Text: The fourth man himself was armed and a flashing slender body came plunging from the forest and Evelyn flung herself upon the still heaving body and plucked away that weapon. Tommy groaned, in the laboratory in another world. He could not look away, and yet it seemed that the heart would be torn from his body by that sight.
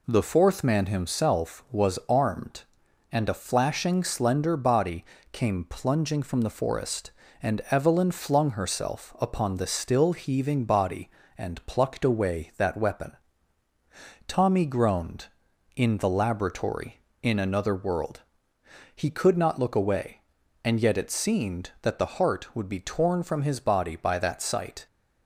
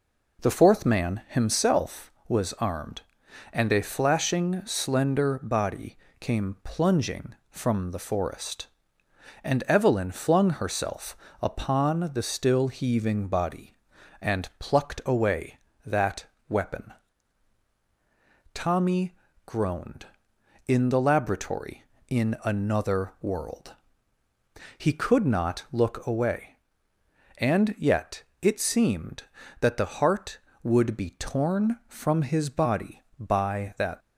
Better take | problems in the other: first | pauses between "body" and "came"; slight; at 5.9 s; 0.24 s long; slight in the first // pauses between "herself" and "upon"; slight; at 11.1 s; 0.28 s long // pauses between "that" and "weapon"; slight; at 16.2 s; 0.24 s long // pauses between "Tommy" and "groaned"; slight; at 19.1 s; 0.32 s long // pauses between "yet" and "it"; slight; at 28.2 s; 0.20 s long // stops before "sight"; at 34.0 s

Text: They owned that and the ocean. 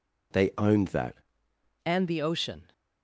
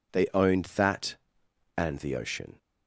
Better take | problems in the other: second | changes voice at "and"; from 1.8 s on; 0.9 s long

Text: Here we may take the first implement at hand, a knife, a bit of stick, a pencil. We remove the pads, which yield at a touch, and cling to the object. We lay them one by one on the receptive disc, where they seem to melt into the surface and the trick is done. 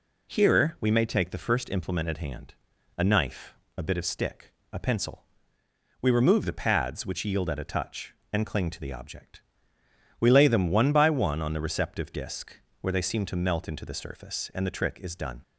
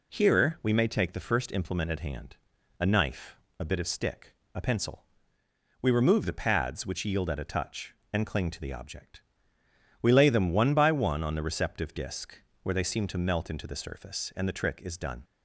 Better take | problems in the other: neither | none

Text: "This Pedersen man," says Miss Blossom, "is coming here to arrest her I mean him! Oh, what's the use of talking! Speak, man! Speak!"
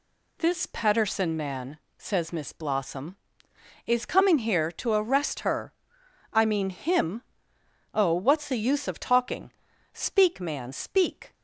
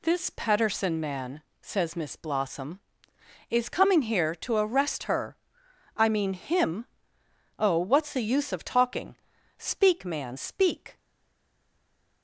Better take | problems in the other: first | pauses between "her" and "I"; noticeable; at 5.3 s; 0.58 s long; noticeable in the first // stays silent after the last word; noticeable; from 10.9 s on; 1.3 s long

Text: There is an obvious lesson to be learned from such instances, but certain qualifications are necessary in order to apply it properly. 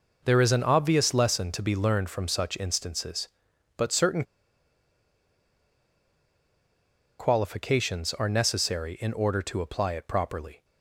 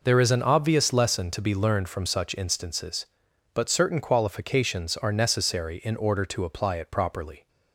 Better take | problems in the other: second | pauses between "certain" and "qualifications"; strong; at 4.2 s; 2.9 s long

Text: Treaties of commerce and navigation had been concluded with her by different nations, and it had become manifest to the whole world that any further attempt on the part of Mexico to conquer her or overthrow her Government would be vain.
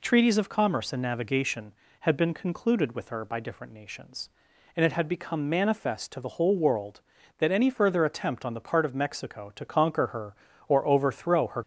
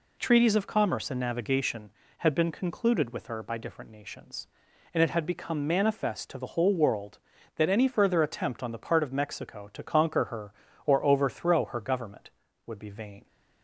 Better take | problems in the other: second | stops before "Government would be vain"; at 11.6 s

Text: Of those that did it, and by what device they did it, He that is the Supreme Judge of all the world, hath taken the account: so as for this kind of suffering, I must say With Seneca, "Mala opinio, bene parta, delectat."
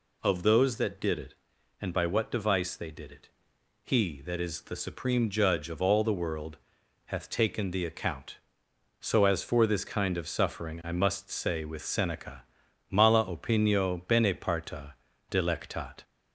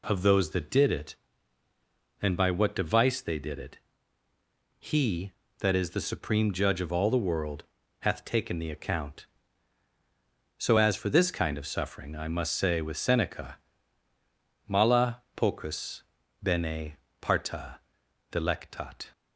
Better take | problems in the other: first | says "pocus" for "opinio"; at 15.3 s // pauses between "bene" and "parta"; slight; at 16.9 s; 0.24 s long

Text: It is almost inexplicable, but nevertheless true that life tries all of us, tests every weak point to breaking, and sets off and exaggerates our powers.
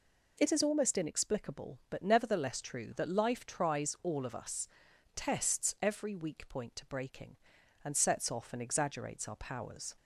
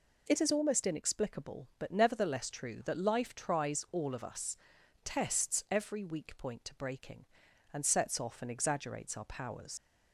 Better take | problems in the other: first | leaves "powers" unfinished; at 9.7 s; 75 ms

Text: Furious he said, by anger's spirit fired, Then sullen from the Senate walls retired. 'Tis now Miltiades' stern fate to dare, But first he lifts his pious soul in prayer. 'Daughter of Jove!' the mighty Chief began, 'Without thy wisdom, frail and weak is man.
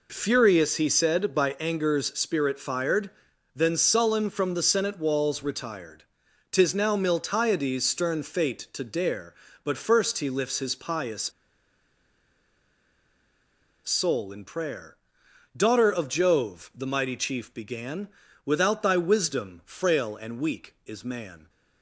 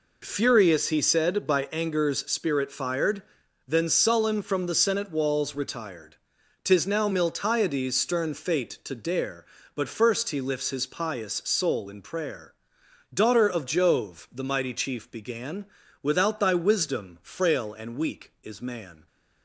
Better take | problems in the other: second | pauses between "pious" and "soul"; strong; at 11.3 s; 2.5 s long

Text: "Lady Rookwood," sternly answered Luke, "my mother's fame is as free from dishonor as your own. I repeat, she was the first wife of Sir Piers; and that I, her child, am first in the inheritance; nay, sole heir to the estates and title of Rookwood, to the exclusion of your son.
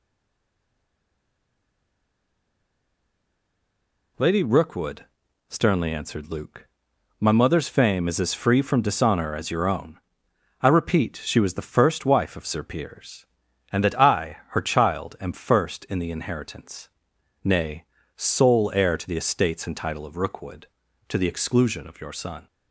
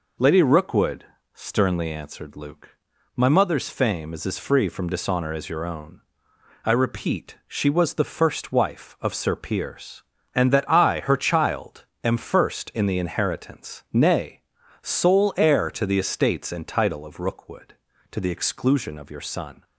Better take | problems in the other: second | stays silent before the first word; strong; until 4.1 s; 4.1 s long

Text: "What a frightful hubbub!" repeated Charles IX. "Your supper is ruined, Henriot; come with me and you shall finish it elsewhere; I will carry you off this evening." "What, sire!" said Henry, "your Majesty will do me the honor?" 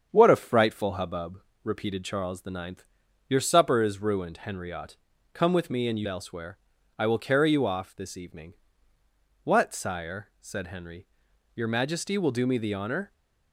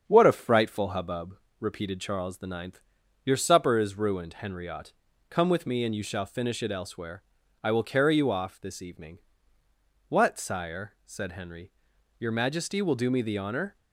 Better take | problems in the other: second | starts louder than the rest; strong; until 1.1 s; 7.5 dB; strong in the second // skips "shall finish it"; at 6.0 s

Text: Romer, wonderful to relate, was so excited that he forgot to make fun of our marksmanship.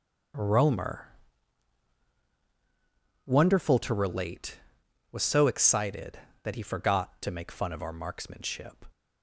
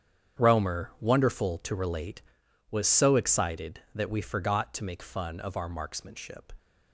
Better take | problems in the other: first | starts louder than the rest; strong; until 1.4 s; 8.5 dB; also in the first // says "we" for "he"; at 4.0 s

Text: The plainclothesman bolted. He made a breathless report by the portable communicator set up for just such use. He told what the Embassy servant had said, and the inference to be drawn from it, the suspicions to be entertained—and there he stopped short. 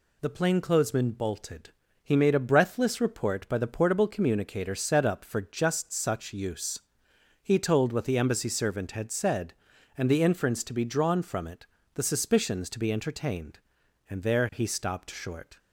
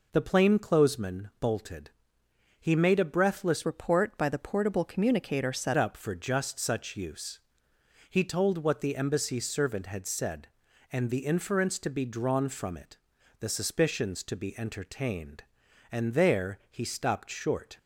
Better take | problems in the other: first | changes voice from "report" to "set"; from 3.6 to 5.7 s; 2.1 s long

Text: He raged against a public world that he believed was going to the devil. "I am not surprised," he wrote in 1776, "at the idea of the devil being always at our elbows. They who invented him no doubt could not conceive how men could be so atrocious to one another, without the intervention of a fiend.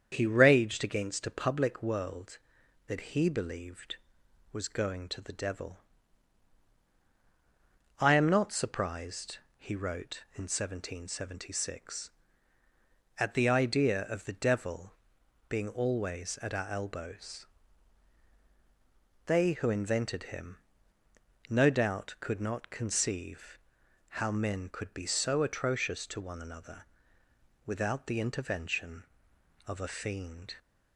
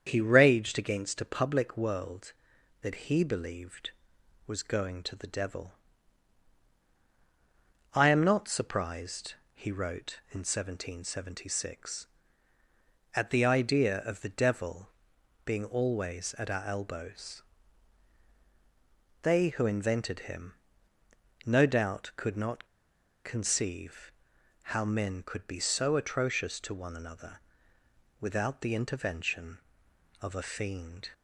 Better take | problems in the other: first | starts louder than the rest; strong; until 1.0 s; 7.5 dB; strong in the first // pauses between "devil" and "being"; noticeable; at 14.8 s; 0.56 s long; noticeable in the first // pauses between "him" and "no"; noticeable; at 20.5 s; 0.92 s long; noticeable in the first // pauses between "not" and "conceive"; noticeable; at 22.6 s; 0.58 s long // pauses between "conceive" and "how"; noticeable; at 24.1 s; 0.62 s long; noticeable in the first

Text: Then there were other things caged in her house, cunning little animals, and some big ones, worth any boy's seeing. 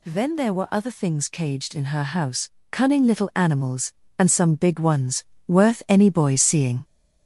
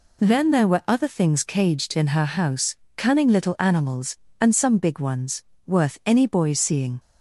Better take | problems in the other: second | gets louder; noticeable; throughout; 4.5 dB

